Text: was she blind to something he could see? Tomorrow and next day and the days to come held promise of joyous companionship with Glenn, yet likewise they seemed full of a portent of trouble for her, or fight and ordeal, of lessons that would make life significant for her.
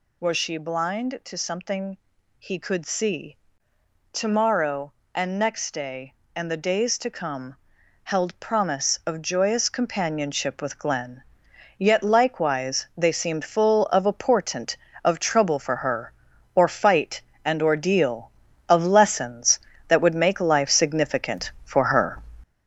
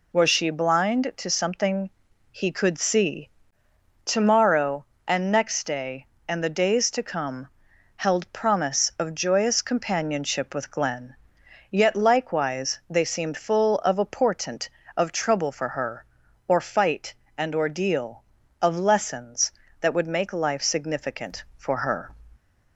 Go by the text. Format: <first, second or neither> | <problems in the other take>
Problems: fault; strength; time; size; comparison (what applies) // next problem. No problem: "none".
second | gets louder; noticeable; throughout; 6 dB // pauses between "something" and "he"; at 1.9 s; 0.42 s long; also in the second // pauses between "come" and "held"; noticeable; at 7.5 s; 0.48 s long; noticeable in the second